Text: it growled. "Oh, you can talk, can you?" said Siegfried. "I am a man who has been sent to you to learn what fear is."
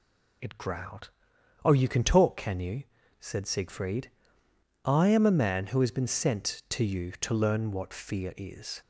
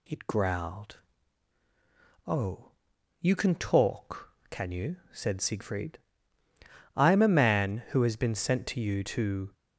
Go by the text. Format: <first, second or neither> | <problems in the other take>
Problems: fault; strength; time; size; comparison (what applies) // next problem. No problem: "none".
first | stops before "learn what fear is"; at 9.5 s